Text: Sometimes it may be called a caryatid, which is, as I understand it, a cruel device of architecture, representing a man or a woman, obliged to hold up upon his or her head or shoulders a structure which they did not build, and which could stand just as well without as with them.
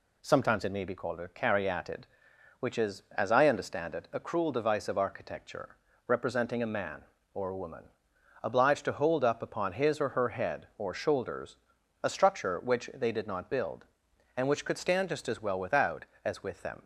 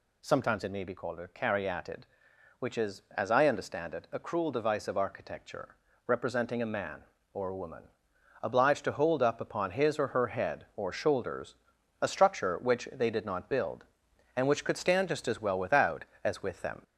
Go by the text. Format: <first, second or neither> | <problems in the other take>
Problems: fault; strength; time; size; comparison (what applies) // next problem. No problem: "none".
first | gets louder; throughout; 3.5 dB // pauses between "shoulders" and "a"; noticeable; at 11.5 s; 0.46 s long; noticeable in the first